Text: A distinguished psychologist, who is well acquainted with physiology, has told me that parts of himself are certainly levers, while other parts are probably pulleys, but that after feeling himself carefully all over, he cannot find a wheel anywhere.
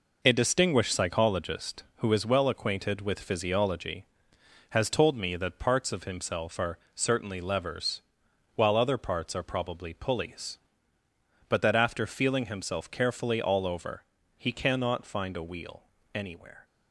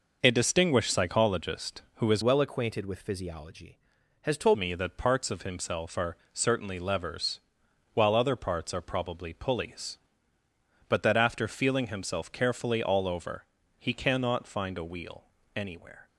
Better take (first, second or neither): first